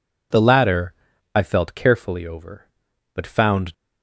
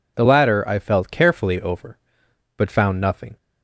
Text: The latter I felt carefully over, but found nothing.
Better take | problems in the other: second | pauses between "latter" and "I"; at 0.9 s; 0.42 s long // stops before "nothing"; at 3.7 s

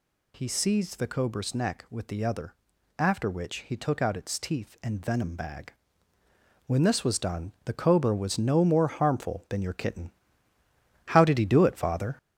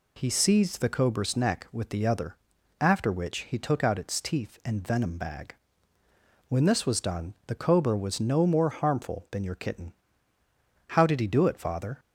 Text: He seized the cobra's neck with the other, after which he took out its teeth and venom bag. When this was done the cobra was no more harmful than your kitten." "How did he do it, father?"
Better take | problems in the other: second | gets louder; noticeable; throughout; 5 dB

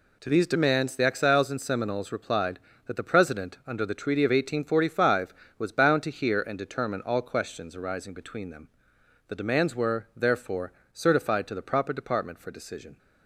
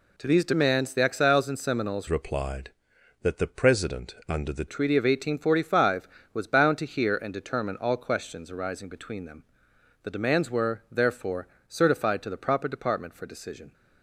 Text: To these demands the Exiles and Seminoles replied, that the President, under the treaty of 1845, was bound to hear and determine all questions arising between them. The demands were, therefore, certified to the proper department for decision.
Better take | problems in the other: first | changes voice from "replied" to "the"; from 2.0 to 4.6 s; 2.6 s long

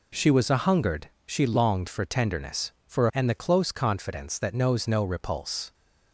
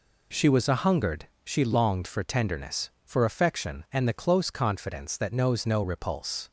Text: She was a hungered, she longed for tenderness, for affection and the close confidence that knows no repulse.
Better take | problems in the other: second | skips "affection"; at 3.1 s

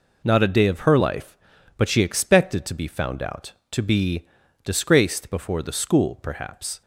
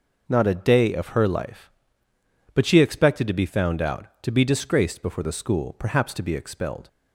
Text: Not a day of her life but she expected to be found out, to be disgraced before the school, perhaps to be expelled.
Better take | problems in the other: second | pauses between "be" and "disgraced"; slight; at 4.2 s; 0.36 s long // stops before "to be expelled"; at 6.8 s

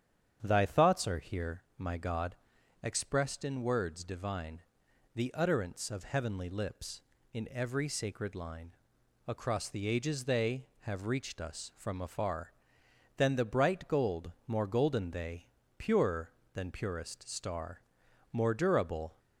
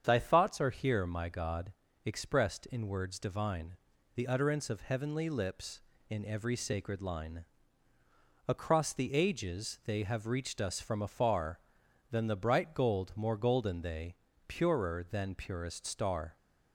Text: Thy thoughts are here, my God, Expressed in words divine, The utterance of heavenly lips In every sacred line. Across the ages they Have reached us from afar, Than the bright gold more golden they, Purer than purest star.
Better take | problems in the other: second | starts louder than the rest; strong; until 1.4 s; 8.5 dB; strong in the second // pauses between "gold" and "more"; slight; at 14.3 s; 0.16 s long // goes on to say "More durable"; noticeable; from 18.3 s on; 0.86 s long

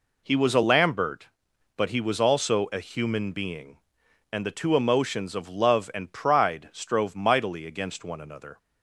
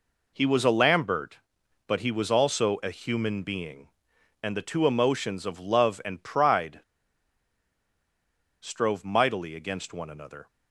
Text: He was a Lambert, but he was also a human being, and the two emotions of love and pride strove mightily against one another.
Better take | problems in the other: first | pauses between "pride" and "strove"; strong; at 6.7 s; 1.8 s long

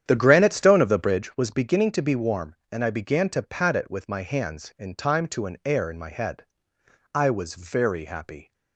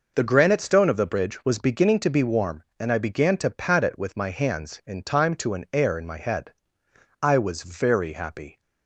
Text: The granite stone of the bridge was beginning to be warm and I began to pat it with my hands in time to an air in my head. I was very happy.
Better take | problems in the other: second | starts louder than the rest; strong; until 1.3 s; 9.5 dB

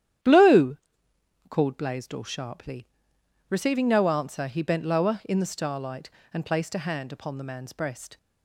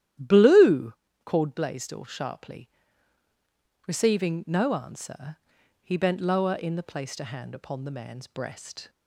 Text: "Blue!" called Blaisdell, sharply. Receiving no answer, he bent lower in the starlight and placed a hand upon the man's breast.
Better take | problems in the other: first | starts louder than the rest; strong; until 1.5 s; 12 dB; strong in the first // skips "starlight and"; at 6.8 s

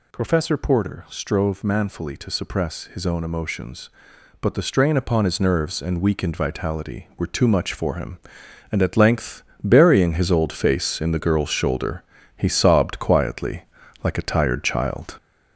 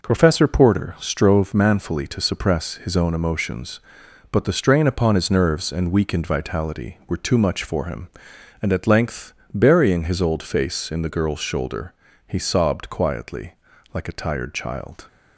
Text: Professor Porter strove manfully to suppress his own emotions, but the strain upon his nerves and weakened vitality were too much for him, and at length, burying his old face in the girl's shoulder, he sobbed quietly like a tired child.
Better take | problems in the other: second | gets louder; noticeable; throughout; 5 dB // pauses between "quietly" and "like"; at 13.6 s; 0.40 s long; also in the second

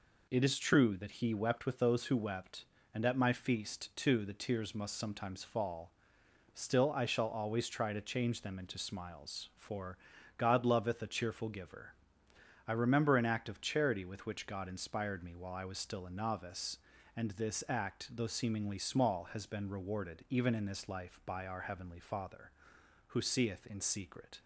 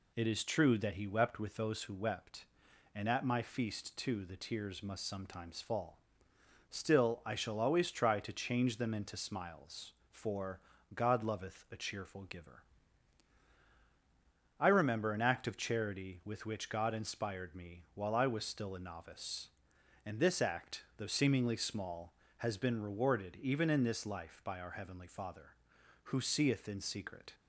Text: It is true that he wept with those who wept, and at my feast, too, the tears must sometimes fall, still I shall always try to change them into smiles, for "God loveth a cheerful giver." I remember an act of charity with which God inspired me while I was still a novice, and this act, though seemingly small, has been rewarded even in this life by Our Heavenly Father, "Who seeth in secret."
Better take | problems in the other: neither | pauses between "for" and "God"; the same in both

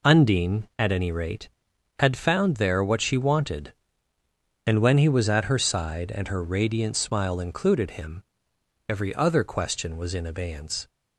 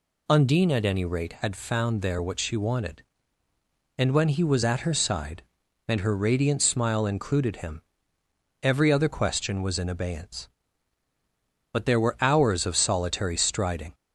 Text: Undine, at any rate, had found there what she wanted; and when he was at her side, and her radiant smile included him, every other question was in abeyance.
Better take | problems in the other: first | goes on to say "But there were hours of solitary striding"; strong; from 11.7 s on; 2.2 s long

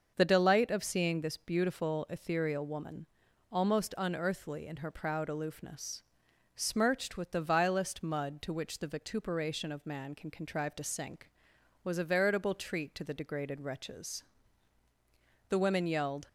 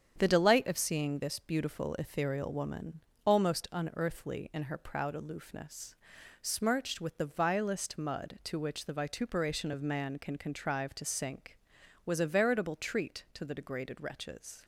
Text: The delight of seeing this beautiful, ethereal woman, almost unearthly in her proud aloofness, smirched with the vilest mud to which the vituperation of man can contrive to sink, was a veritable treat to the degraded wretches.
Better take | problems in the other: second | starts louder than the rest; until 1.1 s; 6.5 dB; strong in the second // goes on to say "The women yelled"; noticeable; from 15.4 s on; 0.80 s long

